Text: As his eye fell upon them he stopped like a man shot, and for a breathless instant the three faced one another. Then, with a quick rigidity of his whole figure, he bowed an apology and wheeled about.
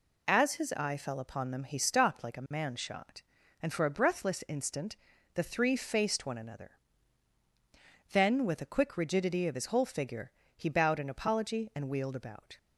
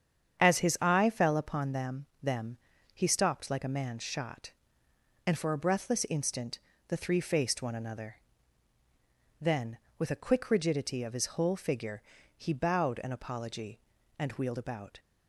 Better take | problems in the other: first | starts louder than the rest; strong; until 1.4 s; 8 dB // says "them" twice; at 2.2 s // pauses between "instant" and "the"; slight; at 6.5 s; 0.30 s long; also in the first

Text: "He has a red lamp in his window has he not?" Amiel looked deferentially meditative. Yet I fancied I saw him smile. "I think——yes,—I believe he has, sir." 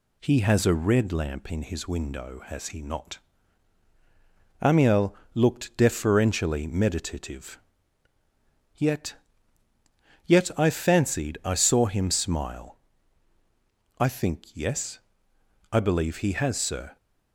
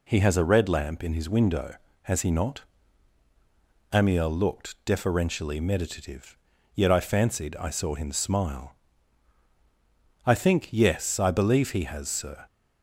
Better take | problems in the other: second | pauses between "Amiel" and "looked"; slight; at 5.1 s; 0.18 s long // says "Yet" twice; at 10.2 s

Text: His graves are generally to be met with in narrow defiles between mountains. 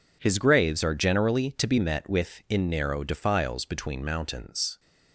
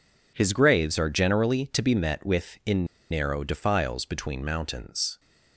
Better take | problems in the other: first | pauses between "in" and "narrow"; slight; at 2.8 s; 0.26 s long

